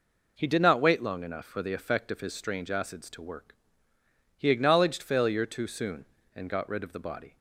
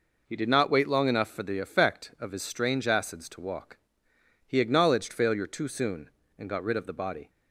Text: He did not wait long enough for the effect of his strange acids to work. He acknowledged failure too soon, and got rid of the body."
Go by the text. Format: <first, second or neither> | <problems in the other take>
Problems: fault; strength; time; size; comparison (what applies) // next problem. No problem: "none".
first | says "walk" for "work"; at 3.3 s